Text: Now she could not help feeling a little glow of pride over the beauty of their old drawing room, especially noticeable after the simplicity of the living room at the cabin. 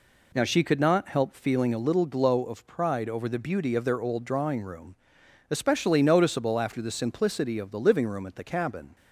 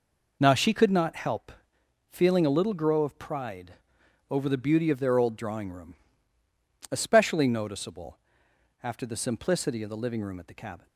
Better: first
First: none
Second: pauses between "help" and "feeling"; noticeable; at 1.5 s; 0.58 s long // says "grow" for "glow"; at 2.7 s // pauses between "pride" and "over"; noticeable; at 3.7 s; 0.58 s long // pauses between "noticeable" and "after"; noticeable; at 8.1 s; 0.64 s long

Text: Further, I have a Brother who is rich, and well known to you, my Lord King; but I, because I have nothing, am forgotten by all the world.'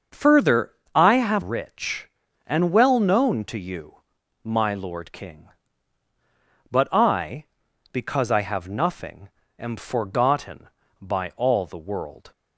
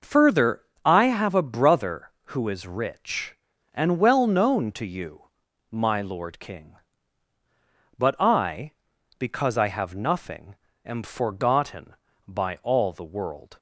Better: second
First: starts louder than the rest; until 1.3 s; 6 dB // skips "a Brother who is"; at 1.4 s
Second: none

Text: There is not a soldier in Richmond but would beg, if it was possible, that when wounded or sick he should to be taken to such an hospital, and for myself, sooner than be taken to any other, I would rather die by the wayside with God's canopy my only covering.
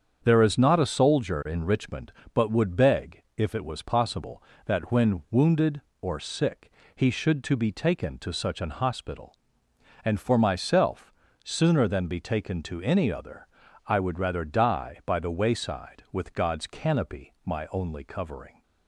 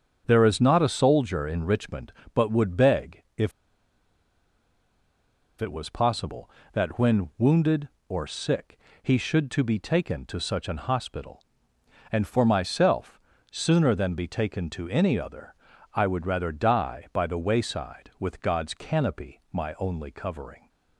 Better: first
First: starts louder than the rest; strong; until 1.2 s; 7.5 dB // pauses between "sick" and "he"; slight; at 6.7 s; 0.24 s long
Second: starts louder than the rest; strong; until 1.2 s; 7.5 dB // pauses between "if" and "it"; strong; at 3.5 s; 2.0 s long // pauses between "sick" and "he"; slight; at 8.7 s; 0.24 s long

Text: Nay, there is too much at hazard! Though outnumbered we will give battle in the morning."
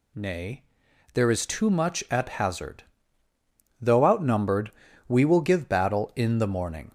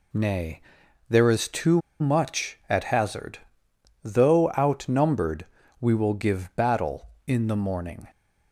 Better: first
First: pauses between "outnumbered" and "we"; slight; at 4.7 s; 0.34 s long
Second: pauses between "too" and "much"; slight; at 1.8 s; 0.19 s long // pauses between "outnumbered" and "we"; slight; at 5.4 s; 0.36 s long

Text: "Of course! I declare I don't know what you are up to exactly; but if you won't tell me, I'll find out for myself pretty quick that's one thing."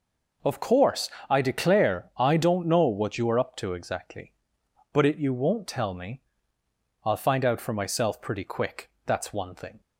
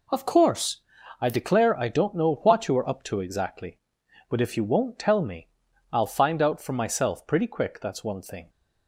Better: second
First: says "it" for "if"; at 5.0 s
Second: none

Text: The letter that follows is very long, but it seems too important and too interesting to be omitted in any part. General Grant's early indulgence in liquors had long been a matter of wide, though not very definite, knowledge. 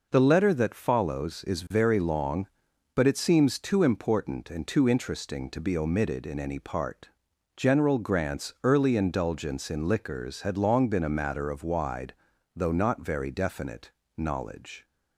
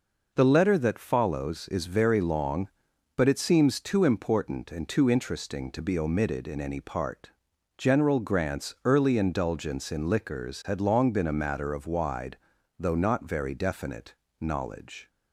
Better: neither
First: none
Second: none

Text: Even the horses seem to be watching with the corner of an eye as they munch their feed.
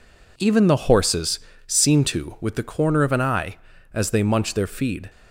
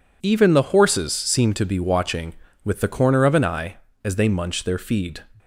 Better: second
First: pauses between "horses" and "seem"; slight; at 1.3 s; 0.26 s long // skips "be watching"; at 2.3 s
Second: none

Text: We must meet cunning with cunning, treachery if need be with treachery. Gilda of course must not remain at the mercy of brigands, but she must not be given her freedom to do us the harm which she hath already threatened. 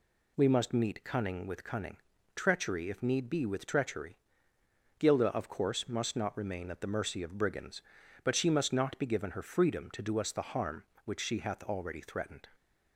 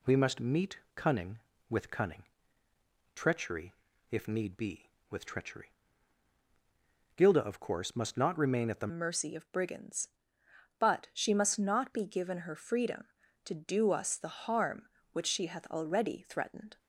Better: first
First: none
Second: pauses between "meet" and "cunning"; slight; at 0.7 s; 0.16 s long // pauses between "treachery" and "if"; at 3.7 s; 0.38 s long // changes voice at "mercy"; from 8.8 s on; 7.9 s long

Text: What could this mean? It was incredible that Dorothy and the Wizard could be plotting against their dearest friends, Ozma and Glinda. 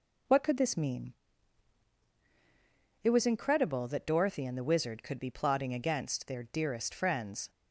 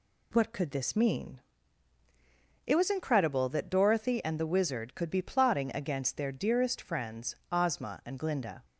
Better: second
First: stops before "Ozma and Glinda"; at 7.4 s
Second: none

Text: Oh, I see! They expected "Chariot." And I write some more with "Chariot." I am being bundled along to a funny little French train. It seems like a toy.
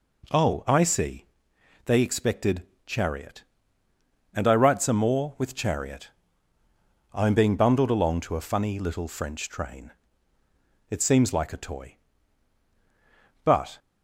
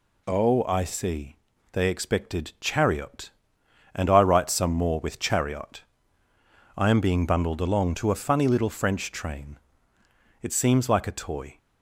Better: second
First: pauses between "expected" and "Chariot"; slight; at 2.6 s; 0.24 s long // goes on to say "But"; slight; from 13.4 s on; 0.34 s long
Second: none

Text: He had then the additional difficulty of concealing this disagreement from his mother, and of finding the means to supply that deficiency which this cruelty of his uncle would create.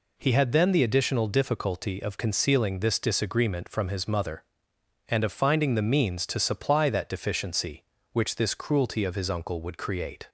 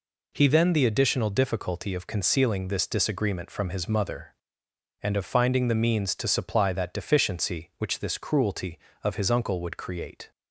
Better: first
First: none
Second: skips "had"; at 0.4 s

